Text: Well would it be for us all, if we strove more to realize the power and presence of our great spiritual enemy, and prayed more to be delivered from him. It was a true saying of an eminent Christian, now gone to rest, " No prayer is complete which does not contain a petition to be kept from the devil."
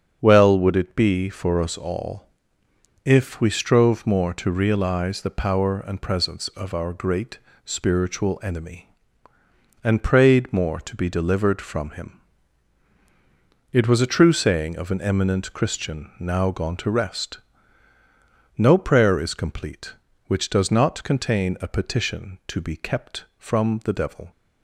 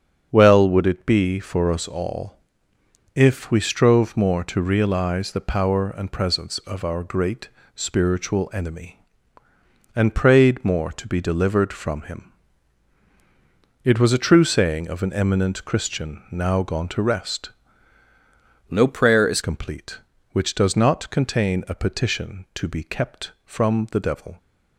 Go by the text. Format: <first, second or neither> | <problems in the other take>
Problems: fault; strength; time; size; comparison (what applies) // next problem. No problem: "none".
first | starts louder than the rest; strong; until 1.3 s; 7.5 dB; strong in the first // pauses between "great" and "spiritual"; slight; at 7.4 s; 0.28 s long; slight in the first // changes voice from "No" to "is"; from 18.6 to 19.3 s; 0.7 s long